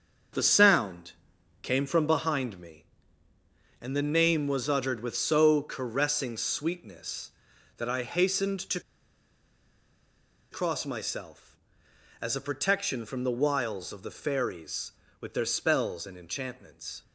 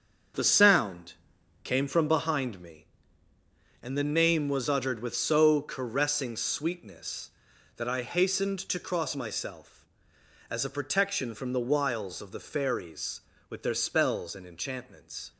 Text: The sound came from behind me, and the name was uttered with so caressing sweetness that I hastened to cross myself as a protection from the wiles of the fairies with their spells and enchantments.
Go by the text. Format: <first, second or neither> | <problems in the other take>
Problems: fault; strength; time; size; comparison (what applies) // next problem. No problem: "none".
second | starts louder than the rest; until 1.8 s; 7 dB; strong in the second // pauses between "sound" and "came"; noticeable; at 1.1 s; 0.50 s long; noticeable in the second // pauses between "to" and "cross"; strong; at 8.7 s; 1.7 s long